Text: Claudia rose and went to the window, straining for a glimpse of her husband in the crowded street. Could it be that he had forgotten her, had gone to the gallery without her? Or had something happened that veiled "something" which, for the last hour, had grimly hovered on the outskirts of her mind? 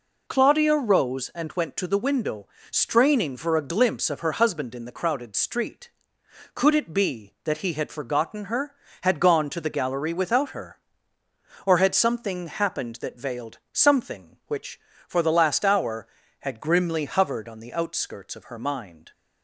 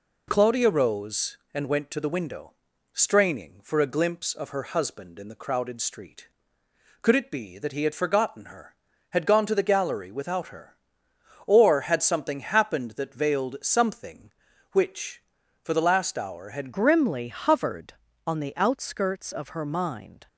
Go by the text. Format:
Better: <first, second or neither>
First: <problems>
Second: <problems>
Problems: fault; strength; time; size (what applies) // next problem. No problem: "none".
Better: first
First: none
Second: changes voice at "grimly"; from 16.7 s on; 3.5 s long